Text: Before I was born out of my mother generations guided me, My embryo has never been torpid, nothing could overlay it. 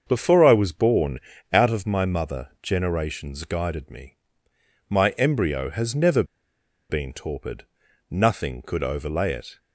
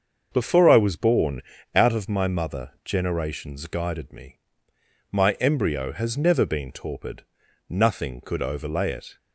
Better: second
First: starts louder than the rest; until 1.0 s; 6.5 dB // pauses between "born" and "out"; slight; at 1.1 s; 0.32 s long // pauses between "never" and "been"; noticeable; at 6.2 s; 0.66 s long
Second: starts louder than the rest; until 1.3 s; 6.5 dB // pauses between "born" and "out"; slight; at 1.4 s; 0.32 s long

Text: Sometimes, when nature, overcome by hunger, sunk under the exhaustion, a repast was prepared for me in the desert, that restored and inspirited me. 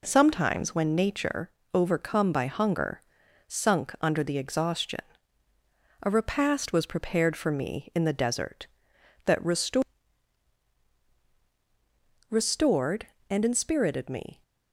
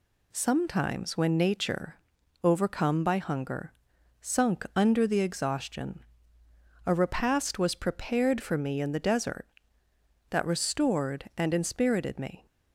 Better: second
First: says "restored" twice; at 12.2 s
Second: none

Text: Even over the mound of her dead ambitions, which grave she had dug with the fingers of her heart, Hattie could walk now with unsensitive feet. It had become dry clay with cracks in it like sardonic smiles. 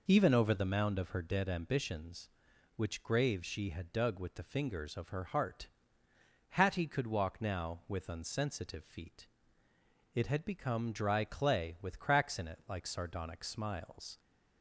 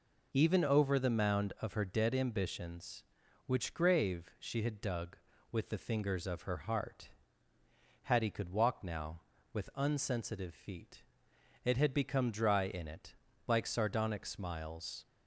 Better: first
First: none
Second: skips "clay with cracks"; at 12.6 s // pauses between "it" and "like"; slight; at 13.1 s; 0.32 s long

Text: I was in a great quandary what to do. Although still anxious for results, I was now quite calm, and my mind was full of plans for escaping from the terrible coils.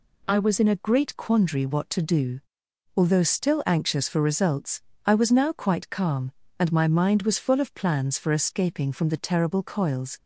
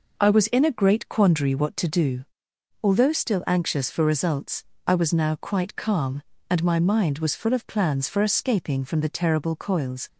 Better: neither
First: none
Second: none

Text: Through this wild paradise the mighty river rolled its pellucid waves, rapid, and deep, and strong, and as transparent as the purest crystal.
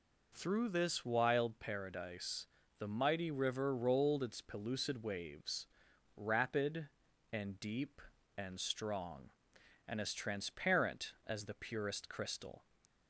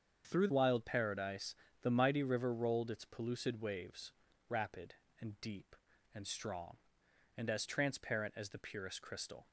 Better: first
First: pauses between "paradise" and "the"; slight; at 2.4 s; 0.32 s long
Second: starts louder than the rest; strong; until 1.3 s; 7 dB // skips "this"; at 0.4 s // pauses between "paradise" and "the"; slight; at 1.5 s; 0.26 s long

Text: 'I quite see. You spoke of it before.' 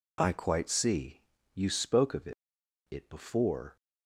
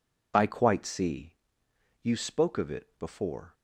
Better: second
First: says "it" twice; at 2.8 s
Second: none

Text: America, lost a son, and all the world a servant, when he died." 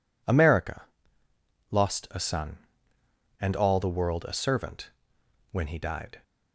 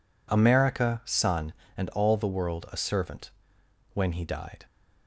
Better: first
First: none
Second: skips "lost a"; at 1.0 s

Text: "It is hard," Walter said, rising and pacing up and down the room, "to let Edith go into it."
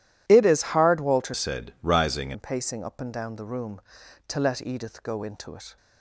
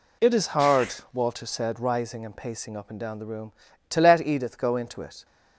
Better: second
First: changes voice from "said" to "rising"; from 1.3 to 2.3 s; 1.0 s long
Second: none

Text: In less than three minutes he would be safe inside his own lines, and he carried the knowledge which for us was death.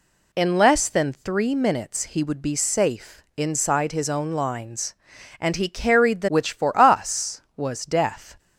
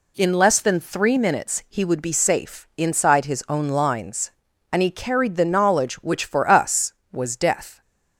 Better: second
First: skips "knowledge"; at 6.2 s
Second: none

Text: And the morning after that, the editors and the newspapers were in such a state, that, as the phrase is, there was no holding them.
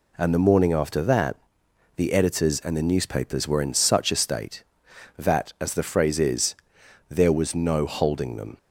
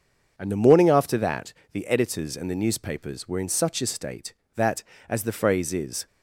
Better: first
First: none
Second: stops before "there was no holding them"; at 6.0 s

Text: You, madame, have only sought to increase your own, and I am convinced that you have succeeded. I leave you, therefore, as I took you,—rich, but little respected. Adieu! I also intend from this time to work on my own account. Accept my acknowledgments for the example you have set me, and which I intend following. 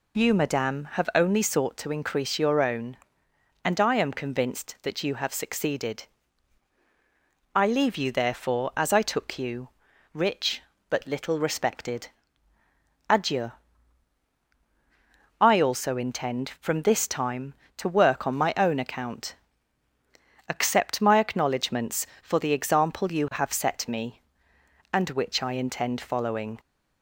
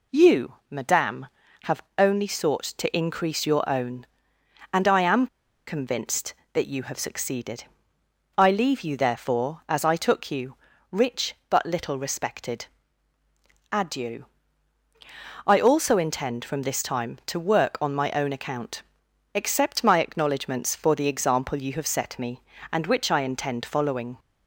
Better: first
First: none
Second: pauses between "have" and "only"; slight; at 1.8 s; 0.16 s long // pauses between "am" and "convinced"; at 5.2 s; 0.40 s long

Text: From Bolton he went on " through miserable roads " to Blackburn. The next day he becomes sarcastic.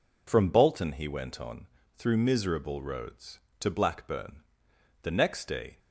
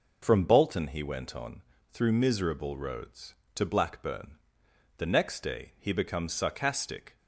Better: second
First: stops before "he becomes sarcastic"; at 5.7 s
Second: none

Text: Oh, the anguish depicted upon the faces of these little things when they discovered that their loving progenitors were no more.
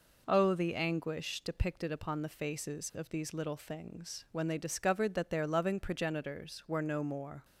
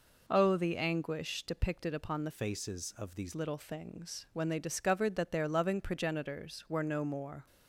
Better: first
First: none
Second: changes voice from "faces" to "these"; from 2.3 to 3.3 s; 1.0 s long

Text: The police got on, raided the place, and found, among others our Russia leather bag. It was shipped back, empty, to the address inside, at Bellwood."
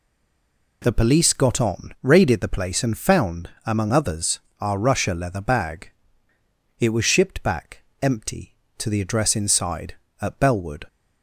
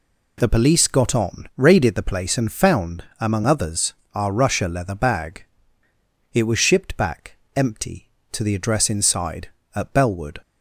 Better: second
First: stays silent before the first word; slight; until 0.8 s; 0.8 s long // pauses between "others" and "our"; slight; at 4.3 s; 0.20 s long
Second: pauses between "others" and "our"; slight; at 3.9 s; 0.20 s long

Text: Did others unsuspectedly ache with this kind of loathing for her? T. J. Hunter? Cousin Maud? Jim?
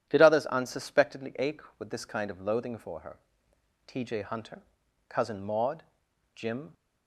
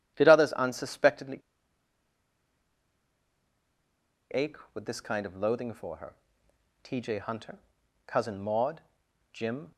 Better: first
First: none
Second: pauses between "unsuspectedly" and "ache"; strong; at 1.4 s; 2.9 s long

